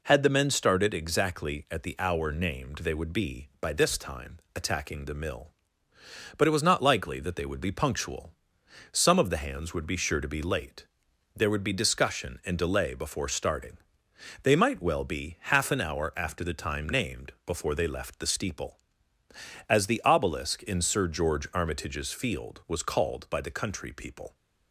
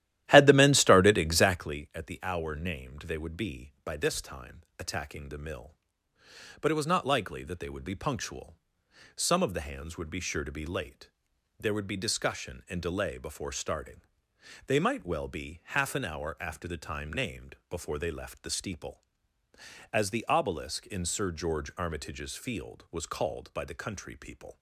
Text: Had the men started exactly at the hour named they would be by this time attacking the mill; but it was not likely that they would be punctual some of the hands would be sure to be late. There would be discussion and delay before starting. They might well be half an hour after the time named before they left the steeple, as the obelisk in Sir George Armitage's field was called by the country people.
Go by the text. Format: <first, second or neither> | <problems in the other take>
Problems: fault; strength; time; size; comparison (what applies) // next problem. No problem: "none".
first | starts louder than the rest; strong; until 1.8 s; 13.5 dB // pauses between "time" and "attacking"; slight; at 4.6 s; 0.18 s long; slight in the first // pauses between "punctual" and "some"; noticeable; at 8.5 s; 0.60 s long; noticeable in the first